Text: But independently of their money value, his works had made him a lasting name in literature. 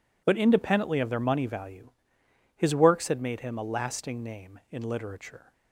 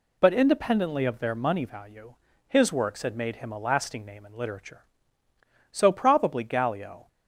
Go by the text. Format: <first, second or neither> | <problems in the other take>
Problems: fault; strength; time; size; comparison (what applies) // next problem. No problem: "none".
first | goes on to say "So probably Gallio"; from 5.6 s on; 1.3 s long